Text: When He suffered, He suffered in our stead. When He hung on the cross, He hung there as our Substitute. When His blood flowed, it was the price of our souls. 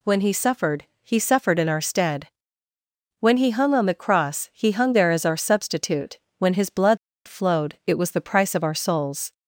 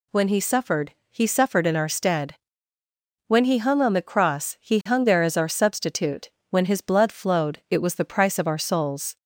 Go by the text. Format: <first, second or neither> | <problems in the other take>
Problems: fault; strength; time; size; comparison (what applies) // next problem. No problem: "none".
second | pauses between "blood" and "flowed"; slight; at 6.9 s; 0.29 s long